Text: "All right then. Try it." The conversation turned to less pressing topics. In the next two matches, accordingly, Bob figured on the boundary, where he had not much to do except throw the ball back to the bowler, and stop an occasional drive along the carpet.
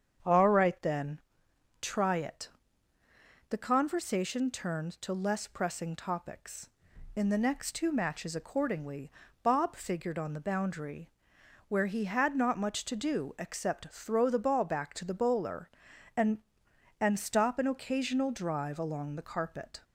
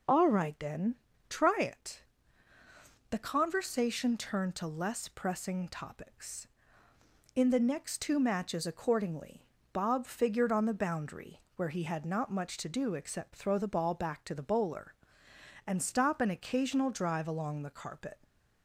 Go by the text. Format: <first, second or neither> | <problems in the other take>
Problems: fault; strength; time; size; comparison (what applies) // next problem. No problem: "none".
second | starts louder than the rest; strong; until 1.8 s; 7.5 dB // says "and" twice; at 16.9 s